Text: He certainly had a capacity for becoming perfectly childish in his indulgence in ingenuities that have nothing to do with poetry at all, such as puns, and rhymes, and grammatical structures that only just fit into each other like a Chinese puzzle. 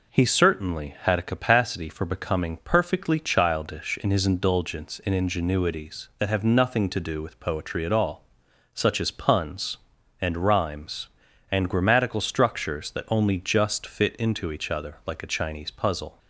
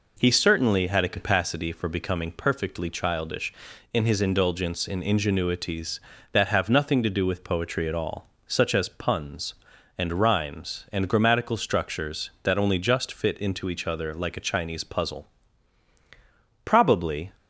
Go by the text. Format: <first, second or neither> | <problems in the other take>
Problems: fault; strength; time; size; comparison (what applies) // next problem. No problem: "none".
first | goes on to say "Probably"; noticeable; from 16.6 s on; 0.66 s long